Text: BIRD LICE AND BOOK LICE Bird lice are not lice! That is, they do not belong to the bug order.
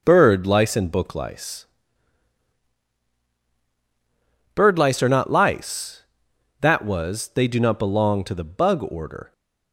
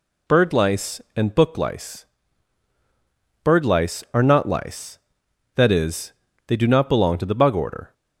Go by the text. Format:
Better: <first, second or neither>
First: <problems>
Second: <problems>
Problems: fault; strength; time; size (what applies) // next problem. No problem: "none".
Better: second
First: pauses between "LICE" and "Bird"; strong; at 1.6 s; 2.9 s long // says "was" for "is"; at 6.8 s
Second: pauses between "LICE" and "Bird"; strong; at 2.0 s; 1.3 s long